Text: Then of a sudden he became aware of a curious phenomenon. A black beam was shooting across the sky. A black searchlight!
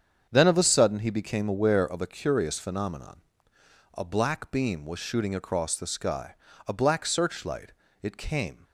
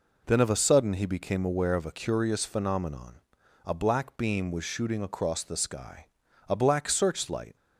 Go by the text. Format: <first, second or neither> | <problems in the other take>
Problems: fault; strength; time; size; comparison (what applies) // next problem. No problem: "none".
second | starts louder than the rest; strong; until 1.3 s; 7.5 dB // goes on to say "It came"; noticeable; from 8.0 s on; 0.62 s long